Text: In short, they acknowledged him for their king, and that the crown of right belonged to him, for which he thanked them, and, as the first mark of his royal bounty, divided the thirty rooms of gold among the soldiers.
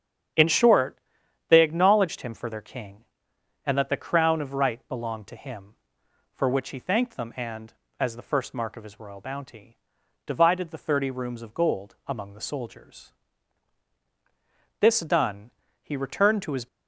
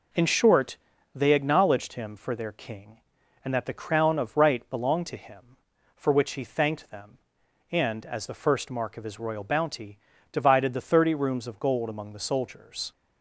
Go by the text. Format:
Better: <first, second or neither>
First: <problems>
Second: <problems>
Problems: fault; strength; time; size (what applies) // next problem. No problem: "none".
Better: second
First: starts louder than the rest; strong; until 1.8 s; 9 dB // goes on to say "This done he returned to his"; strong; from 14.7 s on; 1.8 s long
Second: none